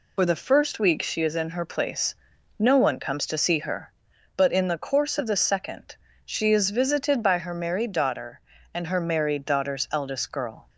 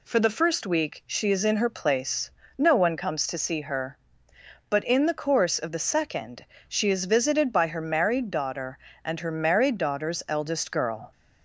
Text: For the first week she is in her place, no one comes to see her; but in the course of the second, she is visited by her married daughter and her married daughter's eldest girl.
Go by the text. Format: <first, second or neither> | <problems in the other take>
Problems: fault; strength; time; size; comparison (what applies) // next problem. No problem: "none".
second | loses the start of "For"; at 0.1 s; 55 ms